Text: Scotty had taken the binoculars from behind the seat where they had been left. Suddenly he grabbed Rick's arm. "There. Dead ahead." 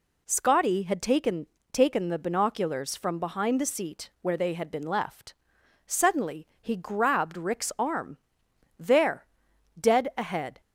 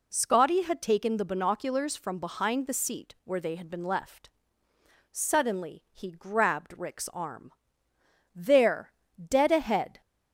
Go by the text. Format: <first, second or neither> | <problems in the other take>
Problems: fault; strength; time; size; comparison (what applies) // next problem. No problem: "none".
second | says "taken" twice; at 1.7 s